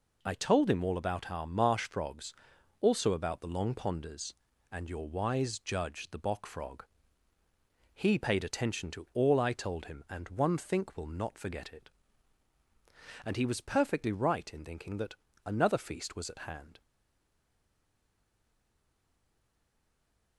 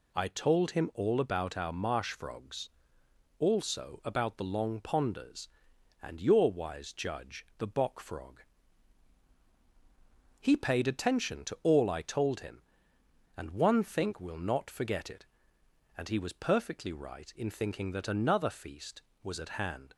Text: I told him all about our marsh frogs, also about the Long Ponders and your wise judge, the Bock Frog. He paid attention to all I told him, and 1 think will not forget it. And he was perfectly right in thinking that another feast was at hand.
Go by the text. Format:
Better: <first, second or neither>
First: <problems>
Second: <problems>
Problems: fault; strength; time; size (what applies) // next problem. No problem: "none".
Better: second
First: pauses between "that" and "another"; slight; at 15.1 s; 0.30 s long // stays silent after the last word; strong; from 16.8 s on; 3.5 s long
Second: none